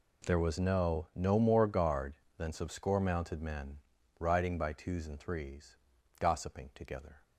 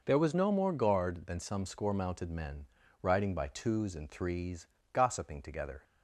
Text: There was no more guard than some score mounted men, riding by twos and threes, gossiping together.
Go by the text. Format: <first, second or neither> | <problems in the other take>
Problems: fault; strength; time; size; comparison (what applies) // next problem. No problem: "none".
second | says "no" twice; at 1.1 s